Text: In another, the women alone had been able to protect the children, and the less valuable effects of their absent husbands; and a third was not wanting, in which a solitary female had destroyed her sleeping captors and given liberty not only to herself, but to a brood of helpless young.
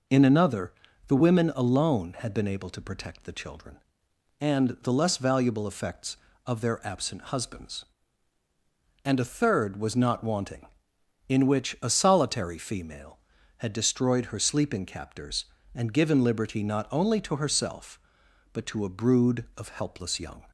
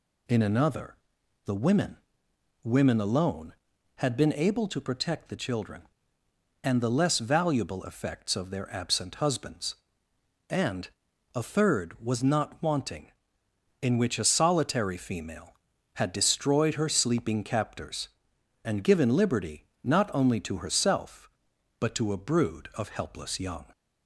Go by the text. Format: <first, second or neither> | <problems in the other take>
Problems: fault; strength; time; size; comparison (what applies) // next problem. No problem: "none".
first | says "women" twice; at 2.6 s // pauses between "and" and "a"; at 10.8 s; 0.44 s long // pauses between "liberty" and "not"; slight; at 19.6 s; 0.20 s long